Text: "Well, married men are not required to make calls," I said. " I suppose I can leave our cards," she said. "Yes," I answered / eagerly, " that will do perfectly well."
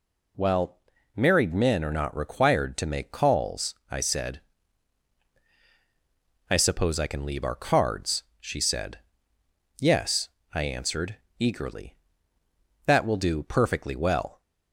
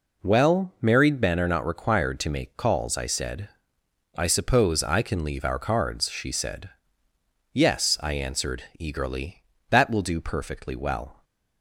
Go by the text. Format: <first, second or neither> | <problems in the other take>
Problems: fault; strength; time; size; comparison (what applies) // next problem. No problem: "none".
neither | none